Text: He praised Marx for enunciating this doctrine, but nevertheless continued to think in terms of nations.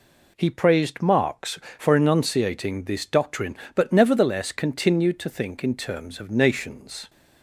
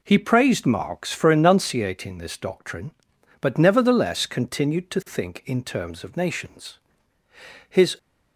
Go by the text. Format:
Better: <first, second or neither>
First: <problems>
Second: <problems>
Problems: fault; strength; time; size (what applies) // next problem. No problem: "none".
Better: first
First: none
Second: goes on to say "His"; slight; from 7.6 s on; 0.30 s long